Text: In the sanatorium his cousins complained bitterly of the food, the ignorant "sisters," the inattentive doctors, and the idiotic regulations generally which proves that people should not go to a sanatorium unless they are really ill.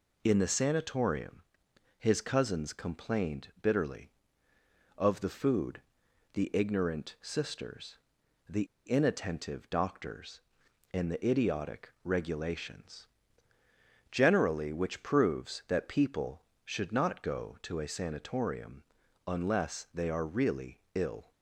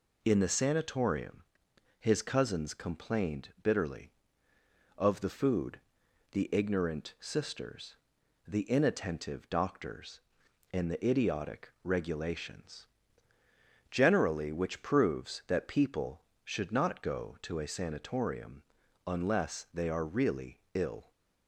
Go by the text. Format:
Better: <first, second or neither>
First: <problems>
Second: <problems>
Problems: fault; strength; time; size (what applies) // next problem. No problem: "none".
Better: second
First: pauses between "sanatorium" and "his"; noticeable; at 1.3 s; 0.58 s long // pauses between "the" and "inattentive"; slight; at 8.6 s; 0.21 s long // pauses between "regulations" and "generally"; at 13.0 s; 1.0 s long // pauses between "sanatorium" and "unless"; at 18.8 s; 0.44 s long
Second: pauses between "sanatorium" and "his"; noticeable; at 1.4 s; 0.58 s long // pauses between "regulations" and "generally"; at 12.8 s; 1.0 s long // pauses between "sanatorium" and "unless"; at 18.6 s; 0.44 s long